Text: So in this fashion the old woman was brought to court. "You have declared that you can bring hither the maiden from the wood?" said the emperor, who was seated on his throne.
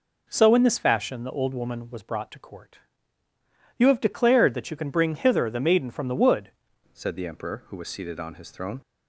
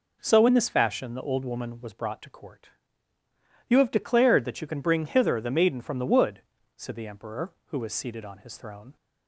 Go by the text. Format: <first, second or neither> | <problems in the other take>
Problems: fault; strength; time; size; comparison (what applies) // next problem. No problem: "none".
second | changes voice at "said"; from 6.9 s on; 1.9 s long